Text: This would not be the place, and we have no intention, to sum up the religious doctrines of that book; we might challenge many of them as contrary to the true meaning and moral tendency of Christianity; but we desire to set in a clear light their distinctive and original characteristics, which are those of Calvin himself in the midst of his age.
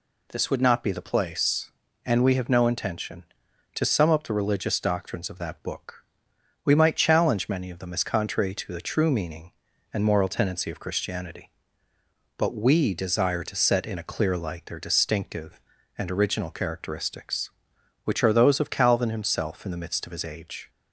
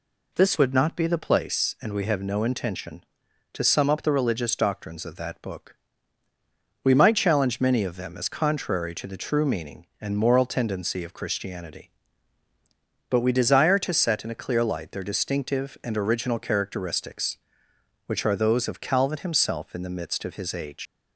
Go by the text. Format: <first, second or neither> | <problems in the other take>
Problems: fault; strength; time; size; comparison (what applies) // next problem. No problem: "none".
first | leaves "age" unfinished; at 20.8 s; 110 ms